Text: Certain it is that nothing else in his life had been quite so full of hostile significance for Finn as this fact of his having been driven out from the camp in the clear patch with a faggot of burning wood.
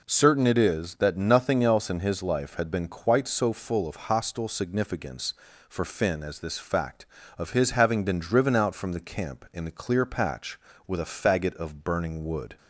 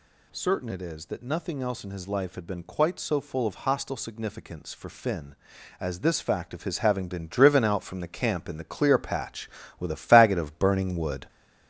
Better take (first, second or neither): first